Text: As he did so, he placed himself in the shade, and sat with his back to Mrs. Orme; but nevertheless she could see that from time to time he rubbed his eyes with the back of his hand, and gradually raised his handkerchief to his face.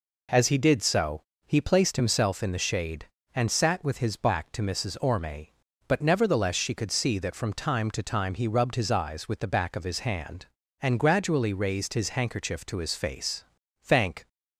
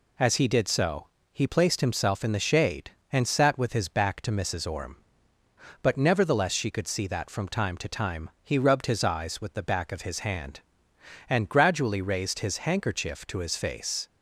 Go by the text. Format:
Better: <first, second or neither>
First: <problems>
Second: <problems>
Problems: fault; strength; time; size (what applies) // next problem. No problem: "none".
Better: second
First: goes on to say "Thank"; slight; from 13.8 s on; 0.46 s long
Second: none